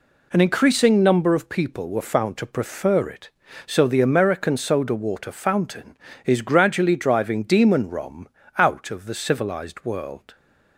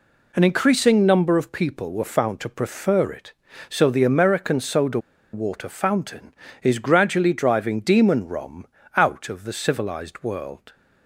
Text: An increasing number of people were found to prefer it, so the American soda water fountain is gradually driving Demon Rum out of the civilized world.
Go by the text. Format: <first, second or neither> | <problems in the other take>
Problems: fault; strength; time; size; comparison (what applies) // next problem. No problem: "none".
first | pauses between "soda" and "water"; slight; at 4.9 s; 0.33 s long // pauses between "Rum" and "out"; slight; at 8.6 s; 0.28 s long; slight in the first